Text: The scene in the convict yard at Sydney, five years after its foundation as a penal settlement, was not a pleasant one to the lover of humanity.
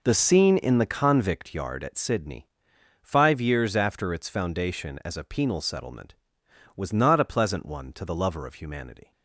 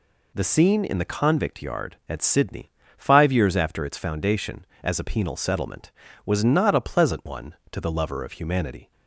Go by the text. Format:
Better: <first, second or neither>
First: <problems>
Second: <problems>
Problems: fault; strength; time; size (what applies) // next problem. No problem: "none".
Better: second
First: starts louder than the rest; noticeable; until 1.4 s; 4.5 dB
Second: none